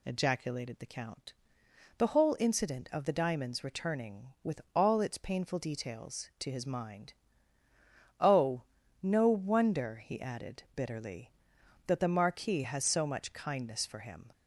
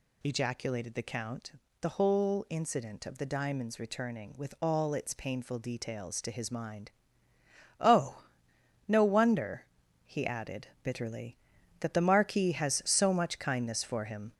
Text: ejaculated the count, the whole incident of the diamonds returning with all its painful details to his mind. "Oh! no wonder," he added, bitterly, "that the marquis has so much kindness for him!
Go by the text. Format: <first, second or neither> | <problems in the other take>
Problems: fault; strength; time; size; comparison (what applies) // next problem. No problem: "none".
first | gets louder; noticeable; throughout; 4.5 dB